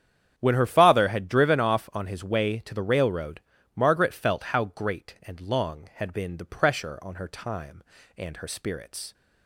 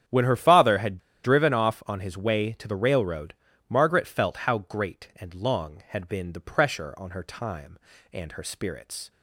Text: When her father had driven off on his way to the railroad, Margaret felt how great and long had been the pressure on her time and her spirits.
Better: first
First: starts louder than the rest; strong; until 1.3 s; 9 dB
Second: starts louder than the rest; strong; until 1.3 s; 9.5 dB // pauses between "had" and "driven"; slight; at 0.9 s; 0.25 s long

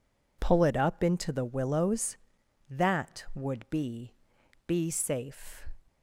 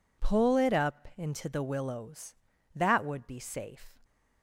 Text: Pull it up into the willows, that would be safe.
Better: second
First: says "be" twice; at 4.6 s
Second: none

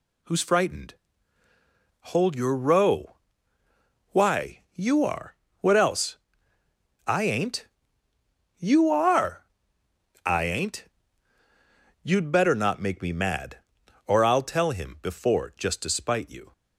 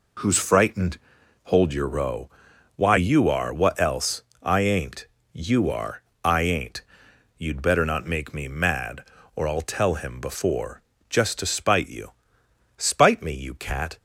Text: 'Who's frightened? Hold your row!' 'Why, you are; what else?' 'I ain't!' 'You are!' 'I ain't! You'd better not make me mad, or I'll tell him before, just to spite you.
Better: first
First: none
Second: goes on to say "Spite me you cat"; noticeable; from 12.7 s on; 1.2 s long

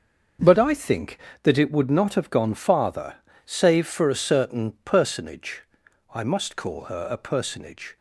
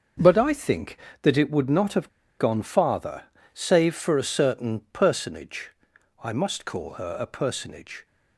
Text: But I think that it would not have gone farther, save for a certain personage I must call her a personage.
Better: first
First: starts louder than the rest; until 1.7 s; 6.5 dB // pauses between "personage" and "I"; noticeable; at 5.6 s; 0.51 s long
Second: starts louder than the rest; until 1.4 s; 6.5 dB // pauses between "have" and "gone"; slight; at 2.0 s; 0.30 s long // pauses between "personage" and "I"; noticeable; at 5.7 s; 0.52 s long

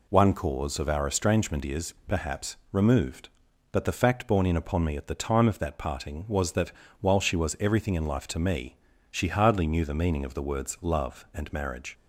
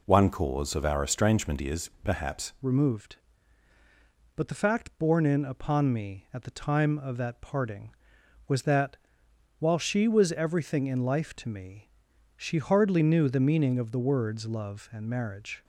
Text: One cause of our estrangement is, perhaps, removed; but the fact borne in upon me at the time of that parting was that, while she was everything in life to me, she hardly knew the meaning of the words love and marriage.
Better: first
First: none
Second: changes voice at "removed"; from 2.6 s on; 13.0 s long

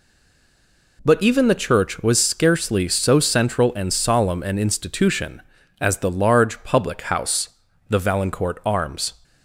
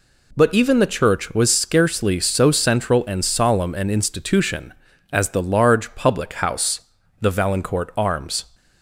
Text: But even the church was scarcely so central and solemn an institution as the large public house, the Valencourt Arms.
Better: second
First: stays silent before the first word; until 0.9 s; 0.9 s long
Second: none

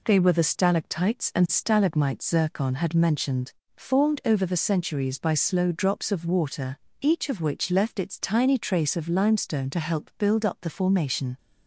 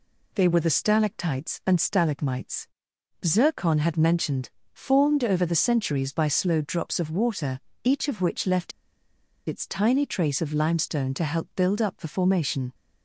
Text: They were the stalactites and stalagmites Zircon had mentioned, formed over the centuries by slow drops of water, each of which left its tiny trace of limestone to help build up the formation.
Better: first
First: none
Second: pauses between "stalagmites" and "Zircon"; noticeable; at 2.6 s; 0.56 s long // pauses between "left" and "its"; noticeable; at 8.7 s; 0.76 s long

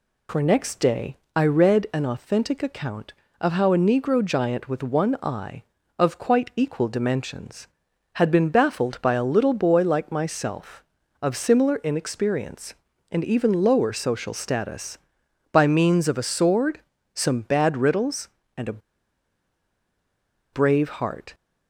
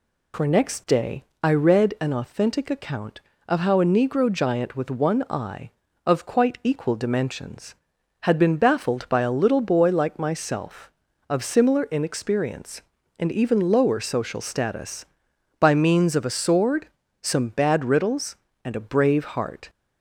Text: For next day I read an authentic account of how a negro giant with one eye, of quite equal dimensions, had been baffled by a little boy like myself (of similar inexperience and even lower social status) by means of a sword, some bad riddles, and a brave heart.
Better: second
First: pauses between "day" and "I"; slight; at 1.1 s; 0.18 s long // pauses between "a" and "brave"; strong; at 18.7 s; 1.7 s long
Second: pauses between "day" and "I"; slight; at 1.2 s; 0.18 s long

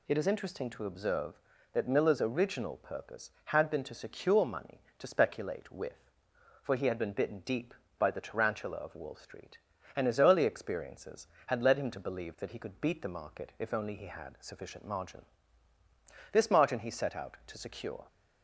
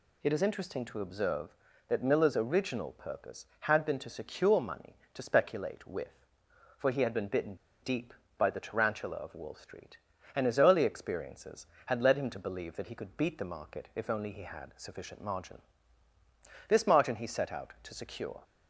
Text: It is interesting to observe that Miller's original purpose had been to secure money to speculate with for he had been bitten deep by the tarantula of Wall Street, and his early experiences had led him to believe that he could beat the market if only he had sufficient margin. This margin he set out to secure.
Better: first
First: none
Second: pauses between "bitten" and "deep"; slight; at 7.5 s; 0.26 s long

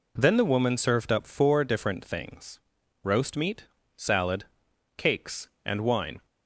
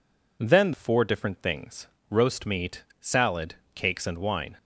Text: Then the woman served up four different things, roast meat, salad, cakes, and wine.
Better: first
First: none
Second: skips "the woman served up"; at 0.7 s

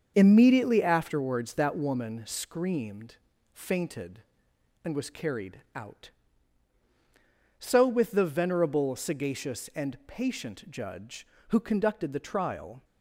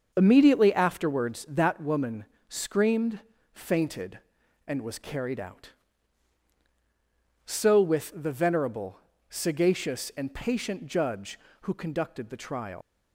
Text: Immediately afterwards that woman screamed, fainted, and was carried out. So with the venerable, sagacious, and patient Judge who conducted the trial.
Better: first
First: starts louder than the rest; until 1.1 s; 6.5 dB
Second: starts louder than the rest; until 1.1 s; 6.5 dB // pauses between "woman" and "screamed"; slight; at 2.2 s; 0.24 s long // leaves "trial" unfinished; at 12.8 s; 115 ms

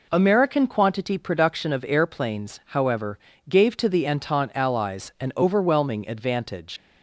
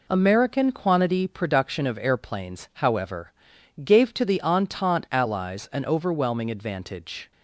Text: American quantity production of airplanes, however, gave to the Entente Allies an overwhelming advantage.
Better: second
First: leaves "advantage" unfinished; at 6.7 s; 100 ms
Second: none

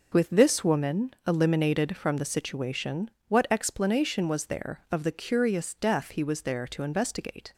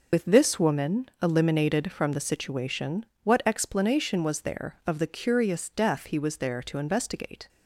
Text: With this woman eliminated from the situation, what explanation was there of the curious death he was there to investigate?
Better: first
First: none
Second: loses the start of "With"; at 0.1 s; 60 ms

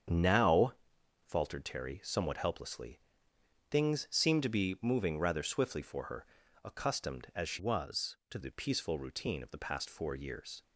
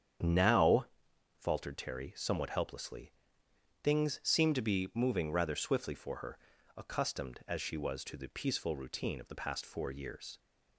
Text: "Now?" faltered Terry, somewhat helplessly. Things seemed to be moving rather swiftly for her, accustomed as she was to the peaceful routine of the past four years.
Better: second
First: starts louder than the rest; strong; until 1.6 s; 8 dB // changes voice from "was" to "to"; from 7.5 to 8.3 s; 0.8 s long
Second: starts louder than the rest; strong; until 1.7 s; 8.5 dB

